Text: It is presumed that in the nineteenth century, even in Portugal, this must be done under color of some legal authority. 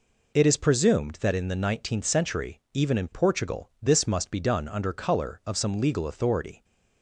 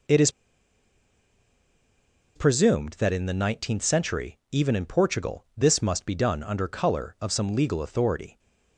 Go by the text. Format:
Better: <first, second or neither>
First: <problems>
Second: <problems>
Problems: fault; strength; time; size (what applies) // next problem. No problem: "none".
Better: first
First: none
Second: pauses between "is" and "presumed"; strong; at 0.3 s; 2.0 s long